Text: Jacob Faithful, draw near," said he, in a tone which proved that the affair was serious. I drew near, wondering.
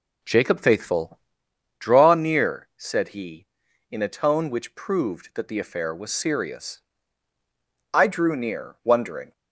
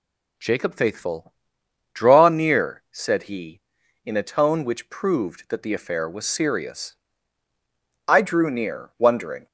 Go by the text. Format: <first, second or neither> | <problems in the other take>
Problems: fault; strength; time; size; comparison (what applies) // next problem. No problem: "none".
second | starts louder than the rest; slight; until 1.3 s; 3 dB